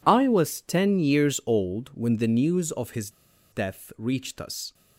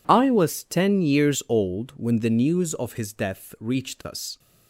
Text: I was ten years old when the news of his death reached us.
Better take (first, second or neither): second